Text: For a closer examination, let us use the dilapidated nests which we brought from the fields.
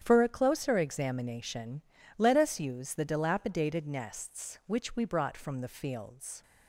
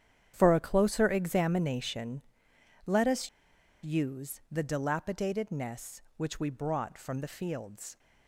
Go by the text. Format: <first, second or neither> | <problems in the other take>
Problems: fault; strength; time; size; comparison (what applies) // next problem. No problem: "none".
first | starts louder than the rest; strong; until 1.3 s; 9 dB; strong in the first // pauses between "us" and "use"; noticeable; at 3.2 s; 0.55 s long